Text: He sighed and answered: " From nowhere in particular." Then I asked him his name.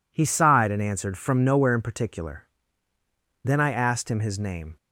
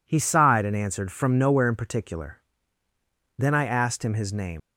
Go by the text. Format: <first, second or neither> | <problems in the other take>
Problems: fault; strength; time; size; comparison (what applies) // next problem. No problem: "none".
first | leaves "name" unfinished; at 4.5 s; 105 ms